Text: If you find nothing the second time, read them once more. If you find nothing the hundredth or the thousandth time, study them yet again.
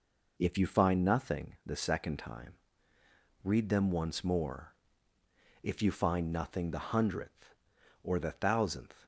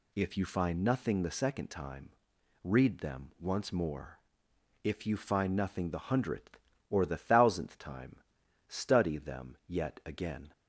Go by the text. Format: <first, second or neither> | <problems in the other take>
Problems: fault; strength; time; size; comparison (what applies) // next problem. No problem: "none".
second | stops before "time study them yet again"; at 9.0 s